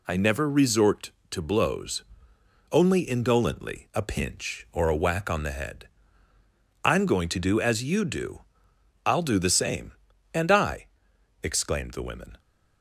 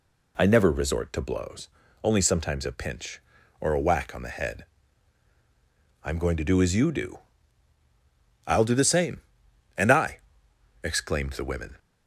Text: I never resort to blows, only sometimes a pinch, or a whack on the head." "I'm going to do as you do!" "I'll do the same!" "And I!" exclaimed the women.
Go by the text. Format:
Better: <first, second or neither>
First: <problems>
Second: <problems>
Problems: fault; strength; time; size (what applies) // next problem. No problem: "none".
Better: second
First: says "indolently" for "sometimes"; at 3.0 s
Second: none